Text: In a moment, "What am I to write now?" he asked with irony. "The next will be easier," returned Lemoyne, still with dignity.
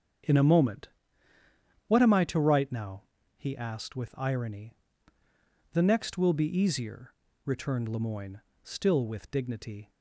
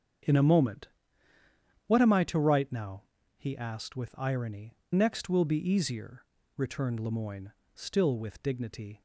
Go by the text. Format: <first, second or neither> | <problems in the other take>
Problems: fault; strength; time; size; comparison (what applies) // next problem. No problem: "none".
first | starts louder than the rest; strong; until 2.2 s; 7 dB; also in the first // skips "The"; at 4.8 s